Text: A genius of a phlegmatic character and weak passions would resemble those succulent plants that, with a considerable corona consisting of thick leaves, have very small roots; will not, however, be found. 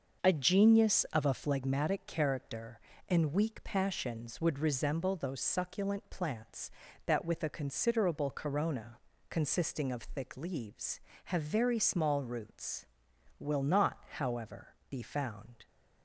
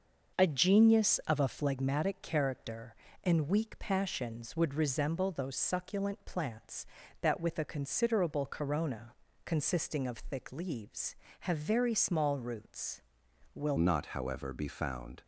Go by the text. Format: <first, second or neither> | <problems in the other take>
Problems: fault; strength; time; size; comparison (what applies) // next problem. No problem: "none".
first | starts louder than the rest; until 1.4 s; 6.5 dB; also in the first // pauses between "corona" and "consisting"; slight; at 9.1 s; 0.32 s long; slight in the first // changes voice at "not"; from 13.7 s on; 1.5 s long